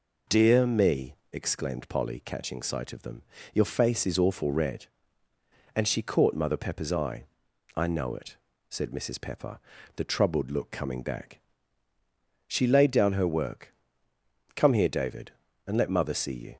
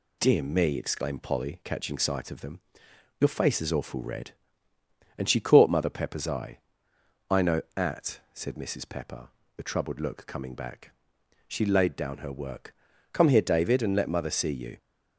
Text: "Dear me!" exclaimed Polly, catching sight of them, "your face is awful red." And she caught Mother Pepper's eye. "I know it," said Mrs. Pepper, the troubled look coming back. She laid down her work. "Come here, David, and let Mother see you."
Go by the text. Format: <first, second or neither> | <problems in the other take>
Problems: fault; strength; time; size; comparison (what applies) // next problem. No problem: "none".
first | says "at" for "it"; at 7.7 s